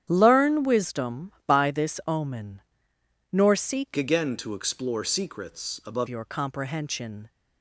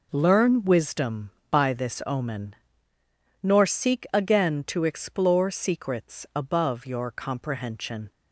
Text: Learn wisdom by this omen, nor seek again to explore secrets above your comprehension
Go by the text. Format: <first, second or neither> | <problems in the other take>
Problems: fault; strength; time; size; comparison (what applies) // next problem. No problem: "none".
second | starts louder than the rest; strong; until 1.1 s; 10 dB // changes voice from "again" to "above"; from 3.9 to 6.0 s; 2.1 s long